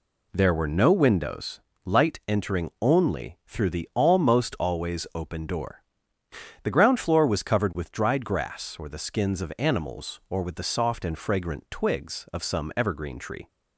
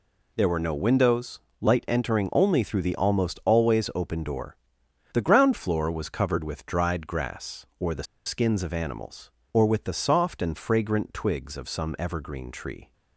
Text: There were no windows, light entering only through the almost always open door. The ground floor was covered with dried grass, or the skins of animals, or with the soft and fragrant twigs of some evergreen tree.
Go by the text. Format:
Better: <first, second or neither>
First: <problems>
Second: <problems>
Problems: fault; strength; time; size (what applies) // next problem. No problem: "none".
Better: first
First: none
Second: pauses between "the" and "skins"; slight; at 8.0 s; 0.22 s long